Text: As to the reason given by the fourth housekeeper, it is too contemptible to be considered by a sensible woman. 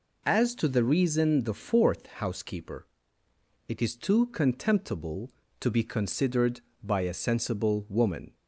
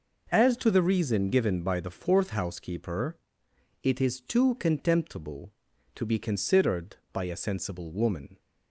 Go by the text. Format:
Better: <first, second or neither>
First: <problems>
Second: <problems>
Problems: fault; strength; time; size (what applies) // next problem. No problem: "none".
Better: second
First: skips "given by"; at 1.4 s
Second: none